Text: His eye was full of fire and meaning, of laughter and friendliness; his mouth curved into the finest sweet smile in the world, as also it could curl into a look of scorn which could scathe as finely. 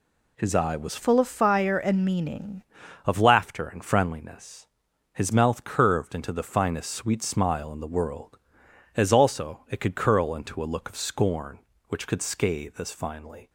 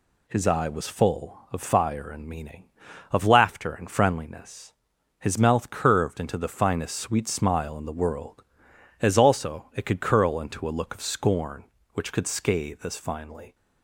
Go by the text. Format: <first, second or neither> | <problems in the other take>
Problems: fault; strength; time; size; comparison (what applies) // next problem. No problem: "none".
second | changes voice from "full" to "meaning"; from 0.9 to 2.6 s; 1.7 s long